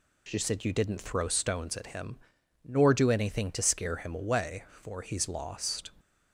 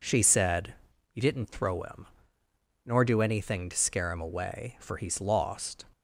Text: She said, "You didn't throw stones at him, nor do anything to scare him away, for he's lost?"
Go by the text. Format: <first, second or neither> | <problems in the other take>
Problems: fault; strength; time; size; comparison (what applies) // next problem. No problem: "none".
first | skips "stones at"; at 1.8 s